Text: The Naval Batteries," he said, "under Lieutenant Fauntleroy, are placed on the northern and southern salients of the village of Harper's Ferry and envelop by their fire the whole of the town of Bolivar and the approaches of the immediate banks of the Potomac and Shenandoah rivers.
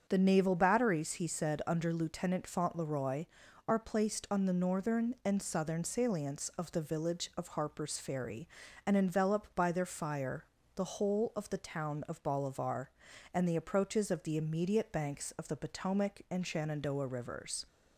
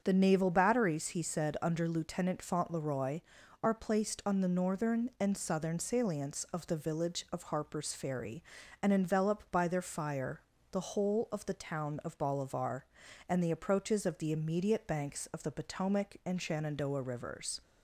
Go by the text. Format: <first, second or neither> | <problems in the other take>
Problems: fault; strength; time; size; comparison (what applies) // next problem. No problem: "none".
neither | starts louder than the rest; the same in both // pauses between "fire" and "the"; slight; the same in both